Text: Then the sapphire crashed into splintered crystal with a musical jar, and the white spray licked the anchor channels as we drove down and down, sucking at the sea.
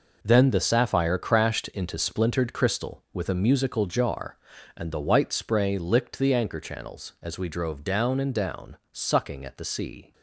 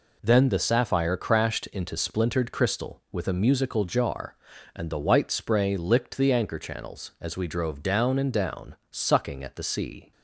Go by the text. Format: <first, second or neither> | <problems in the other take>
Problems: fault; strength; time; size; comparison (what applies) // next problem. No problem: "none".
second | gets quieter; strong; throughout; 9.5 dB